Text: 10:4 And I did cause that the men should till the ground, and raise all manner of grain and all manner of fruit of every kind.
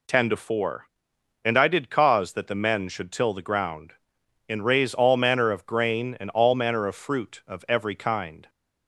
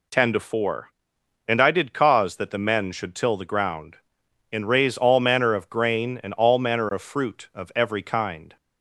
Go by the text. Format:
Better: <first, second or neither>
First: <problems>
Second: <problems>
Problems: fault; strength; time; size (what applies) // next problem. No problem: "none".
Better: neither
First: none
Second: none